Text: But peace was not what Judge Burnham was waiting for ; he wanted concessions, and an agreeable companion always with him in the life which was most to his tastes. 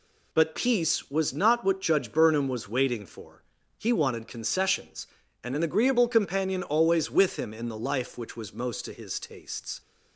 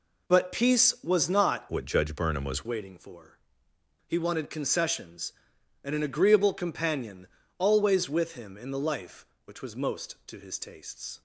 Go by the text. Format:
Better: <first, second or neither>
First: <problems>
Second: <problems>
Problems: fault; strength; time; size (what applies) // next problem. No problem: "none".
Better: first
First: none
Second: changes voice from "what" to "was"; from 1.7 to 2.6 s; 0.9 s long // pauses between "companion" and "always"; slight; at 7.2 s; 0.32 s long